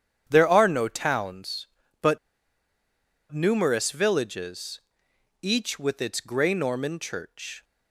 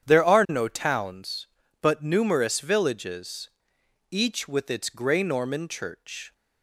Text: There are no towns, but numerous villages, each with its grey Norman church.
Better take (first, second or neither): second